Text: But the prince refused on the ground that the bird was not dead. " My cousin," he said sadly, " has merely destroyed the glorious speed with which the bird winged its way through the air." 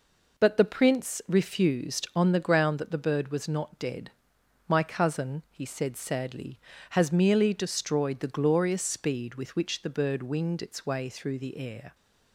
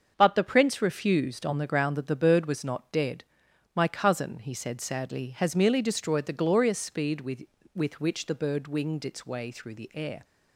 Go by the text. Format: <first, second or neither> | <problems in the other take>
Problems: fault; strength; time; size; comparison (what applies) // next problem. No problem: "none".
first | starts louder than the rest; until 1.1 s; 7 dB // says "with" twice; at 7.7 s